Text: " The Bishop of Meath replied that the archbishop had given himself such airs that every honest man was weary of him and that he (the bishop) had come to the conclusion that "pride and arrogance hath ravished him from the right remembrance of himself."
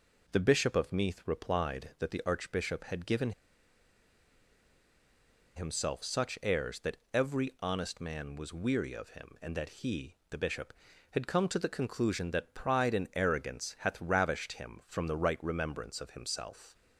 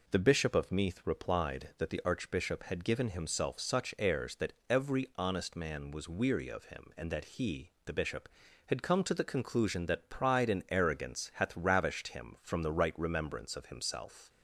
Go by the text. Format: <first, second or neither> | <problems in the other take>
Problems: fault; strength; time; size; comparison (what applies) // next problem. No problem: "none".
second | pauses between "given" and "himself"; strong; at 3.3 s; 2.2 s long // pauses between "that" and "every"; slight; at 6.9 s; 0.18 s long; slight in the second